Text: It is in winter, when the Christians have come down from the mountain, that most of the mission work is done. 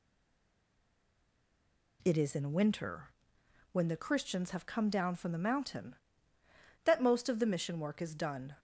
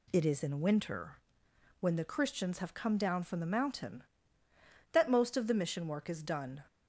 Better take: second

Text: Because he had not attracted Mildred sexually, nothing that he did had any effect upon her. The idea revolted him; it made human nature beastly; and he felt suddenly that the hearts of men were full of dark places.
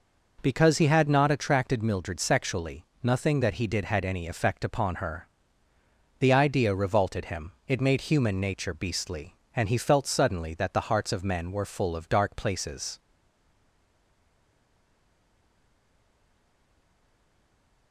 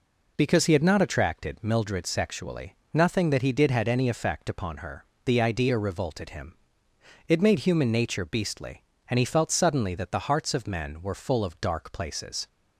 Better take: second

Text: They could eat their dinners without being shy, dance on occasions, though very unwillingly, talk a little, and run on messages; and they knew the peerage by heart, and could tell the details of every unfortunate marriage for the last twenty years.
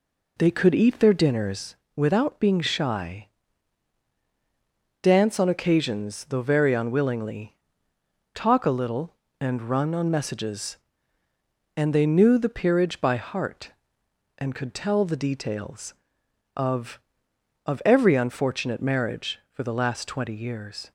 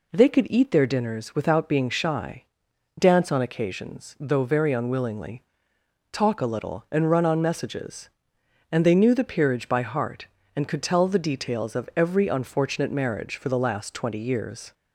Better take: second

